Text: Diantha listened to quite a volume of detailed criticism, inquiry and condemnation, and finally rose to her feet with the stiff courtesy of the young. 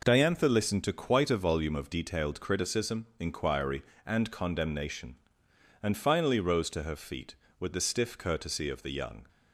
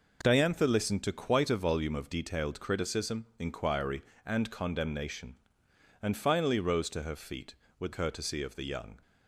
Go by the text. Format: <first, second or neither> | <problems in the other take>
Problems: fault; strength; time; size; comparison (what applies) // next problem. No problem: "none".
first | skips "the stiff"; at 7.9 s